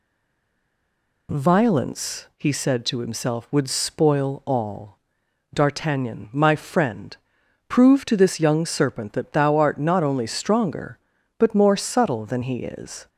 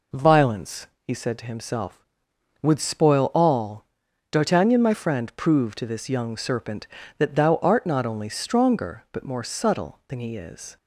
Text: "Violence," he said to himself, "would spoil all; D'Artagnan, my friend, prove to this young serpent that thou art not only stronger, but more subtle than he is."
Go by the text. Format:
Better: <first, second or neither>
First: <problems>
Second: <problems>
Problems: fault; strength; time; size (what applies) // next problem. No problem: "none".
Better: second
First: stays silent before the first word; noticeable; until 1.2 s; 1.2 s long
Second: none